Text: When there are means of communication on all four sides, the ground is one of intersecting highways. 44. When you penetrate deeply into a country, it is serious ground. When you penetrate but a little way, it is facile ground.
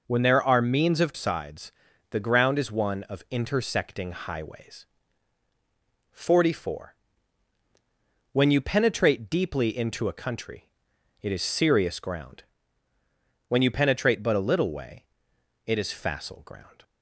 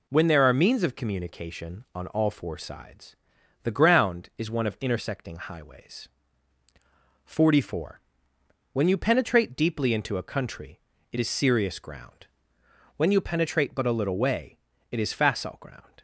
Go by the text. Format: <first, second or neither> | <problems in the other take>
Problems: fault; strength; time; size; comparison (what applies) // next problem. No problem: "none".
second | skips "communication on all four"; at 1.1 s